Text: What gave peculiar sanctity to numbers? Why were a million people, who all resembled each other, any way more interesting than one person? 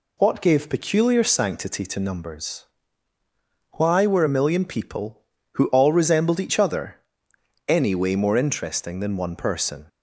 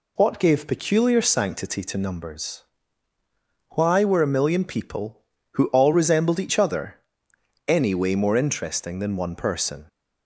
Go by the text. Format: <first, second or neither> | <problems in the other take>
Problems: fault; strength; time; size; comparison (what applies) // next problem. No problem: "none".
neither | none